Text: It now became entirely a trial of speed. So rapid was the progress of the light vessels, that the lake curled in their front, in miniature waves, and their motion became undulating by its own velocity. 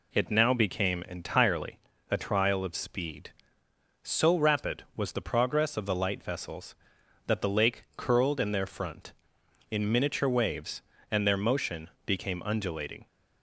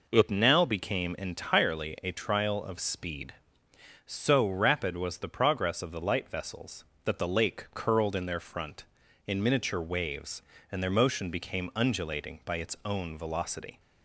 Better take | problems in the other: second | pauses between "entirely" and "a"; slight; at 1.7 s; 0.32 s long // pauses between "motion" and "became"; slight; at 11.8 s; 0.16 s long // stops before "by its own velocity"; at 13.0 s

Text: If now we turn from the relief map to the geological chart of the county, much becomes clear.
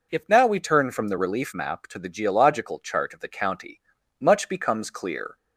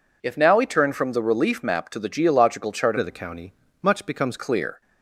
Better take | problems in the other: first | changes voice from "of" to "becomes"; from 2.9 to 4.3 s; 1.4 s long

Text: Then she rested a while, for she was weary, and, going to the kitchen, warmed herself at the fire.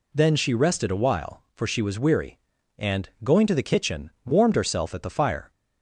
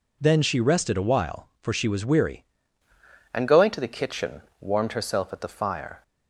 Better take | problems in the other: first | changes voice at "and"; from 3.3 s on; 2.7 s long

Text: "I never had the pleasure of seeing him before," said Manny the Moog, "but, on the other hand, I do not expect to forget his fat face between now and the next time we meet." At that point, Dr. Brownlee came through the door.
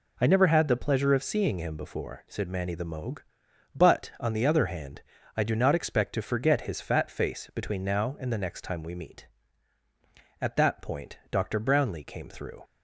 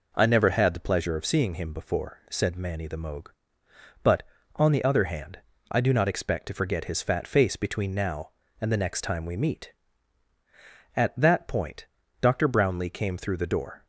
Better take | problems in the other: second | stops before "the door"; at 12.6 s

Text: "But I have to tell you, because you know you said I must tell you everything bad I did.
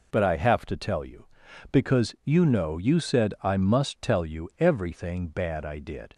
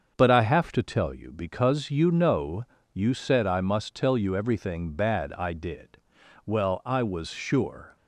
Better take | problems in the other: first | starts louder than the rest; until 1.2 s; 6.5 dB // pauses between "know" and "you"; slight; at 2.6 s; 0.26 s long // goes on to say "Well I was sure"; from 6.4 s on; 1.5 s long

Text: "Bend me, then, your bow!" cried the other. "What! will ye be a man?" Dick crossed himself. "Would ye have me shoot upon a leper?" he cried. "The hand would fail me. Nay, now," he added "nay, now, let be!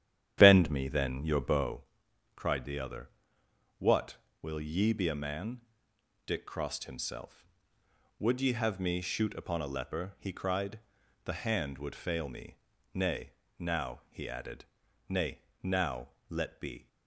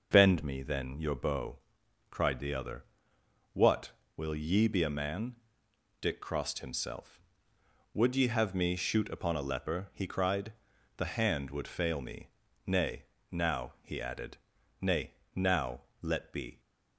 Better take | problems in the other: second | starts louder than the rest; strong; until 1.8 s; 10.5 dB // pauses between "added" and "nay"; at 14.6 s; 0.44 s long; also in the second

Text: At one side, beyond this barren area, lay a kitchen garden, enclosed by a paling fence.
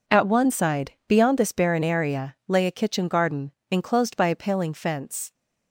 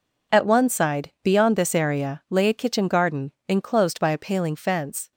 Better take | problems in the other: first | skips "barren"; at 1.7 s

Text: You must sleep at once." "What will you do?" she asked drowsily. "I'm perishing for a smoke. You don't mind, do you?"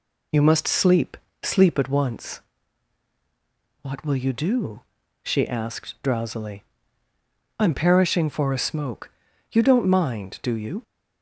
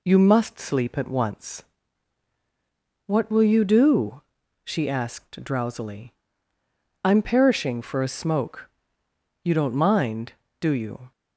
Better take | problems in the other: second | says "sleep" twice; at 1.4 s

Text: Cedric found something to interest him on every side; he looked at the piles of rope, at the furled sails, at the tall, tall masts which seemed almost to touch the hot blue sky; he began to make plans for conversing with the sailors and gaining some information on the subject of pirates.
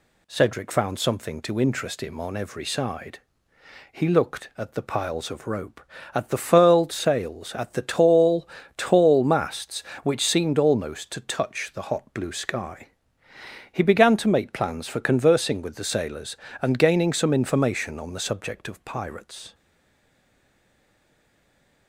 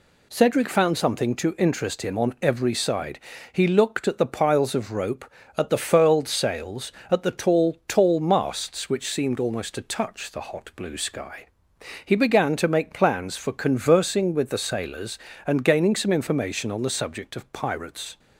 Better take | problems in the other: second | stays silent after the last word; from 19.5 s on; 2.3 s long

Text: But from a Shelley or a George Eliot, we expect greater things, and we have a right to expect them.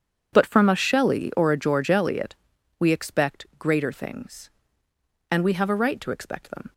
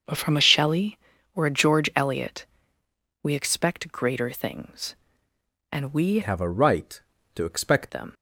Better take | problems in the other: first | starts louder than the rest; until 1.4 s; 6.5 dB // changes voice from "have" to "expect"; from 6.2 to 7.9 s; 1.7 s long

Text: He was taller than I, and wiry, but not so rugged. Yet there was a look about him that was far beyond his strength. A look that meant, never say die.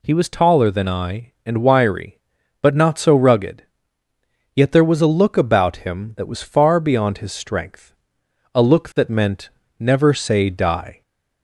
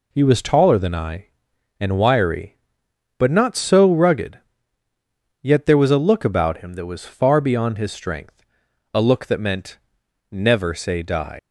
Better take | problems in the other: first | leaves "die" unfinished; at 11.3 s; 125 ms

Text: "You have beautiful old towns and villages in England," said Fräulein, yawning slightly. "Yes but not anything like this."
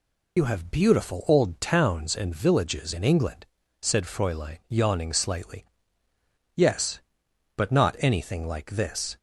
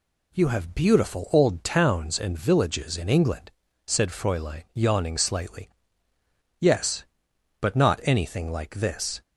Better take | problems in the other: second | loses the start of "You"; at 0.3 s; 80 ms

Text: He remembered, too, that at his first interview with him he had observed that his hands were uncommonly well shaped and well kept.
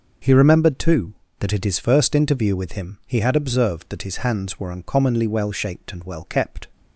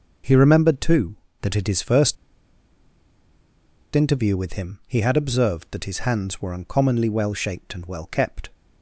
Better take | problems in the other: first | pauses between "first" and "interview"; strong; at 2.1 s; 1.7 s long

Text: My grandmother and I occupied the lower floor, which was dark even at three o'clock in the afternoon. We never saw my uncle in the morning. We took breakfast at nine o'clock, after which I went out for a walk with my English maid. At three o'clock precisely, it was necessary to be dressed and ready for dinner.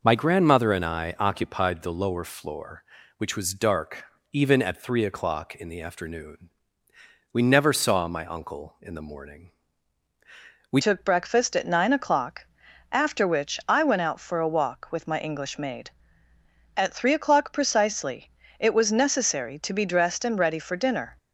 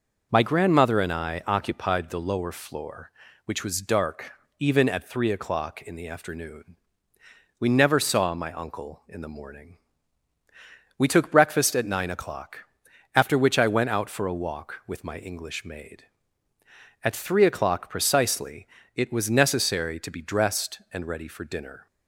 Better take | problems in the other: second | pauses between "dark" and "even"; slight; at 4.0 s; 0.28 s long; slight in the second // changes voice at "took"; from 10.8 s on; 10.3 s long

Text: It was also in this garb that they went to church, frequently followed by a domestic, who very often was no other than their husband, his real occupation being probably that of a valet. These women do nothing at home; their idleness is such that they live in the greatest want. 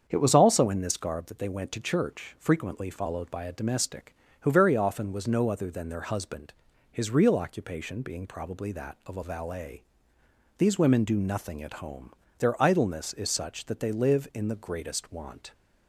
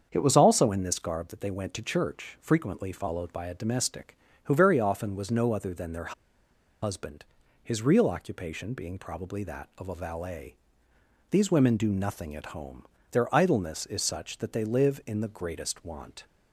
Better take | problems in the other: first | starts louder than the rest; strong; until 1.1 s; 7 dB; strong in the first // pauses between "their" and "husband"; noticeable; at 6.1 s; 0.69 s long

